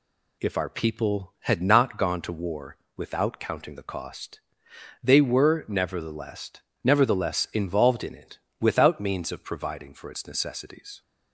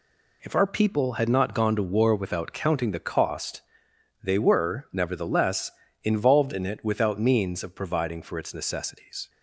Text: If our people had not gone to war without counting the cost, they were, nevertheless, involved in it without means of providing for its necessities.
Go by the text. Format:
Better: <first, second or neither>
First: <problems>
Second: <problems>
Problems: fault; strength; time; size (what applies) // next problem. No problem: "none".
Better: second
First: pauses between "war" and "without"; slight; at 2.7 s; 0.20 s long // says "nevertheless" twice; at 6.8 s // pauses between "it" and "without"; slight; at 8.3 s; 0.22 s long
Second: none